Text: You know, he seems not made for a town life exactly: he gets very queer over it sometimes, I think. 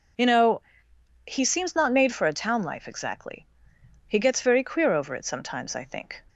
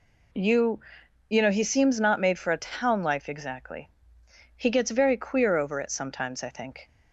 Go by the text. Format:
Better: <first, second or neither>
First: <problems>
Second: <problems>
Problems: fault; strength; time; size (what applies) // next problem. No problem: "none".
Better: first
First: none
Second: says "You" twice; at 1.2 s